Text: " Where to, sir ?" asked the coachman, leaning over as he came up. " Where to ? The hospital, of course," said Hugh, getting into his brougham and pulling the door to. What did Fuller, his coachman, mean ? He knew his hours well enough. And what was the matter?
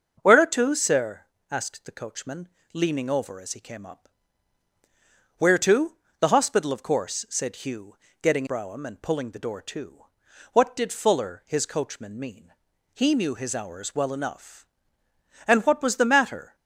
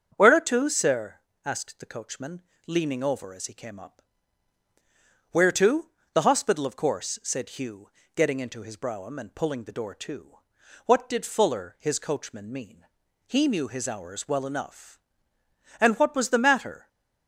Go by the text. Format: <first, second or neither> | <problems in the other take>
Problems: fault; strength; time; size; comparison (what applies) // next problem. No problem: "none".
second | starts louder than the rest; strong; until 1.1 s; 7.5 dB; strong in the second // skips "into his"; at 8.4 s